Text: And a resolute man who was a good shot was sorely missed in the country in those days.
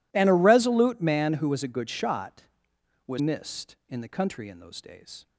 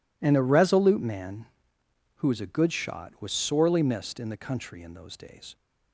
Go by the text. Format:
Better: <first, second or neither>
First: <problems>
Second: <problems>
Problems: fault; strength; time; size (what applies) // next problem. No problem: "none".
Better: second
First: skips "sorely"; at 3.1 s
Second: none